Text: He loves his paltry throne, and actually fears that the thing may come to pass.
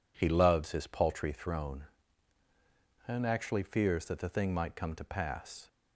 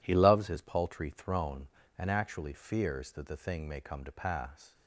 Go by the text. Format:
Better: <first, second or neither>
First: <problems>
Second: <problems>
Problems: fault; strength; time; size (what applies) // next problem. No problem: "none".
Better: second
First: says "might" for "may"; at 4.5 s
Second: none